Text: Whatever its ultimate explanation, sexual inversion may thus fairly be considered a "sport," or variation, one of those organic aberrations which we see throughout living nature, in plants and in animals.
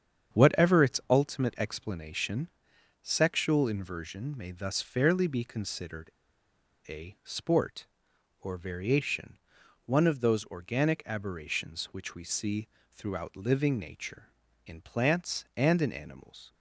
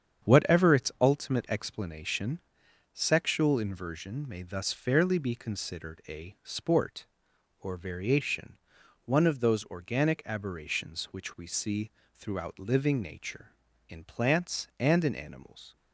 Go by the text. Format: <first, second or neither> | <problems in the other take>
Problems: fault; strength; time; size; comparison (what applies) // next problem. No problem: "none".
second | starts louder than the rest; strong; until 1.4 s; 8 dB; strong in the second // pauses between "considered" and "a"; noticeable; at 6.0 s; 0.79 s long // pauses between "see" and "throughout"; slight; at 12.6 s; 0.24 s long; slight in the second